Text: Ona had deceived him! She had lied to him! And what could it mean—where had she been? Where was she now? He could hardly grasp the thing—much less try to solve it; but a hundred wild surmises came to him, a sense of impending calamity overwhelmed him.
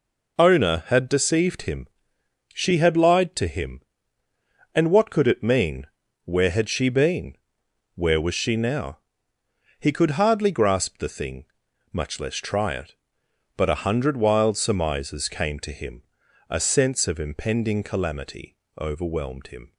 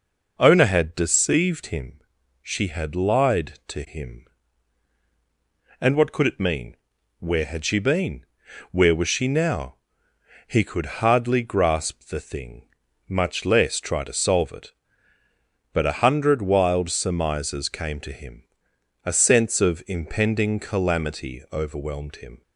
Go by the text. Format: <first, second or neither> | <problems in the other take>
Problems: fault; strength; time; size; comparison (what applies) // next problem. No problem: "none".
second | skips "to solve"; at 12.7 s // pauses between "calamity" and "overwhelmed"; slight; at 18.5 s; 0.24 s long